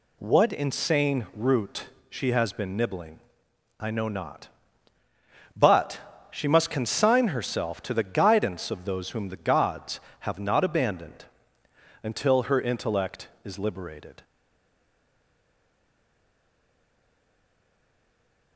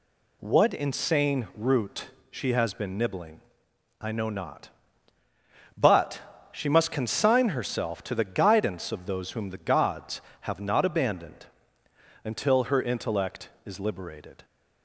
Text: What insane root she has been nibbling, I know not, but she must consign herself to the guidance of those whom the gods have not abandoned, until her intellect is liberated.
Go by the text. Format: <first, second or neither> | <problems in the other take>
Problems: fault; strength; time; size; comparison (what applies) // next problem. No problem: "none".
second | pauses between "root" and "she"; slight; at 1.8 s; 0.24 s long; slight in the second // stays silent after the last word; strong; from 14.2 s on; 4.3 s long